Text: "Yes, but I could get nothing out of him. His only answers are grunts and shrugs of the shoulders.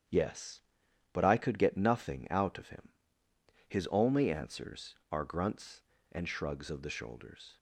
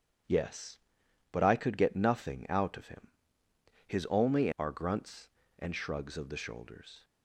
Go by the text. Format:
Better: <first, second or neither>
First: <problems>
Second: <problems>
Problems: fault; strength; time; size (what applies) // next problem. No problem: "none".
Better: first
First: starts louder than the rest; strong; until 1.6 s; 9 dB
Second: starts louder than the rest; strong; until 1.8 s; 9 dB // skips "answers"; at 4.5 s